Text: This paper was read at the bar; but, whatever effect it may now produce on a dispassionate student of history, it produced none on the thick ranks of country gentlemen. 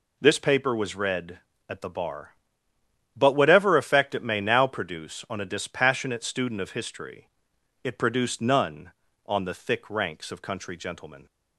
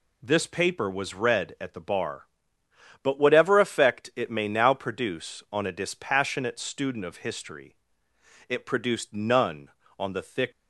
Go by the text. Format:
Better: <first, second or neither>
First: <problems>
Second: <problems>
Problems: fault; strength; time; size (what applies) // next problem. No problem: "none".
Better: first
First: none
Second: stops before "ranks of country gentlemen"; at 10.5 s